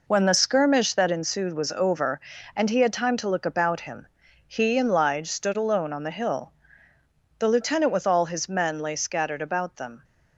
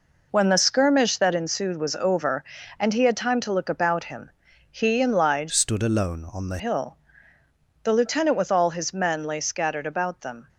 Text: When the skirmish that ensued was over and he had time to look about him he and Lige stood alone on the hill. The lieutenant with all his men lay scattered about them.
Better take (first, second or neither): first